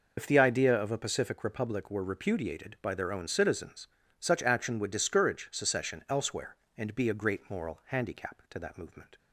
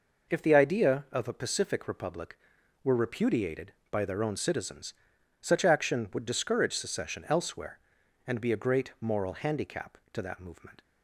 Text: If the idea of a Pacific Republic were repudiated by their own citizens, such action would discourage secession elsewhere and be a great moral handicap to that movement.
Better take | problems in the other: second | loses the start of "If"; at 0.1 s; 40 ms

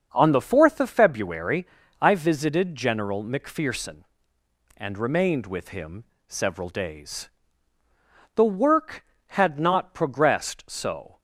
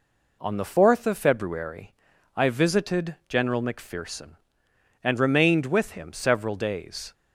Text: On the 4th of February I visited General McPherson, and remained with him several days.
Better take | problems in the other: second | starts louder than the rest; until 1.1 s; 6.5 dB // pauses between "February" and "I"; slight; at 1.6 s; 0.34 s long; also in the second // pauses between "him" and "several"; slight; at 6.0 s; 0.22 s long // goes on to say "The work had not progressed so"; strong; from 8.3 s on; 2.8 s long

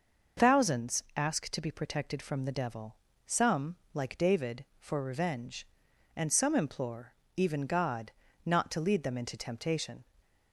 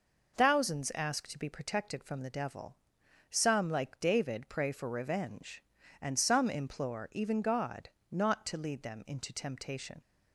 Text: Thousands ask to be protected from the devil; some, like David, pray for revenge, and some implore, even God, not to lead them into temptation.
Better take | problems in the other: second | starts louder than the rest; noticeable; until 1.5 s; 6 dB // skips "pray"; at 4.7 s

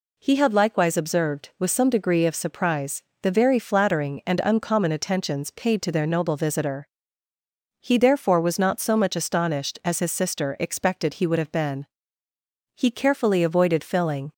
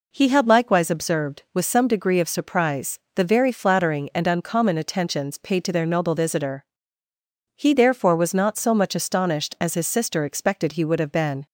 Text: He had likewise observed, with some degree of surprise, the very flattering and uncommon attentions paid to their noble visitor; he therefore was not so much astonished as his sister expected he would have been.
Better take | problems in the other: second | goes on to say "He carefully avoided filling"; from 12.7 s on; 1.5 s long

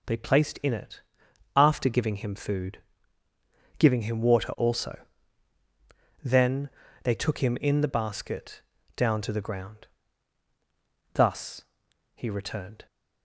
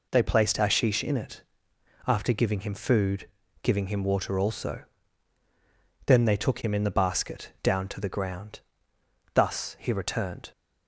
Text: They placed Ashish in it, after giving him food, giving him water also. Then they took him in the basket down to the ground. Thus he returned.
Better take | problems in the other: second | skips "Ashish"; at 0.5 s // pauses between "Then" and "they"; slight; at 6.6 s; 0.34 s long // pauses between "basket" and "down"; slight; at 8.6 s; 0.34 s long // pauses between "Thus" and "he"; noticeable; at 11.6 s; 0.50 s long

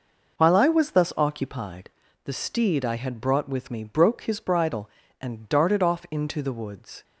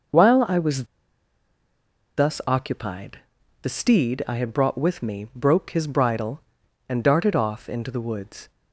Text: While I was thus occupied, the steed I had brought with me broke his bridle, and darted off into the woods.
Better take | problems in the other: first | pauses between "was" and "thus"; strong; at 0.8 s; 1.3 s long

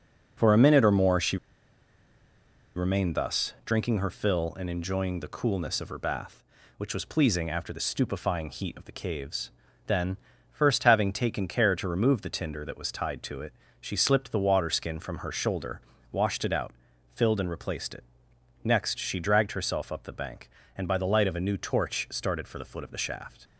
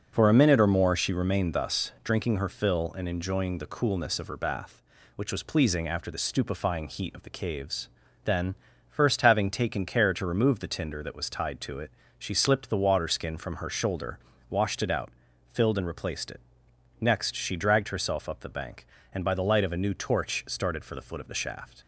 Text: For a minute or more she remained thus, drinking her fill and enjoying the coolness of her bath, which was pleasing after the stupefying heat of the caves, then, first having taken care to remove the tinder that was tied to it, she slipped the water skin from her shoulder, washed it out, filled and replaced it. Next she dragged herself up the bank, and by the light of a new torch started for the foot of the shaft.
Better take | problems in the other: second | pauses between "she" and "remained"; strong; at 1.3 s; 1.3 s long

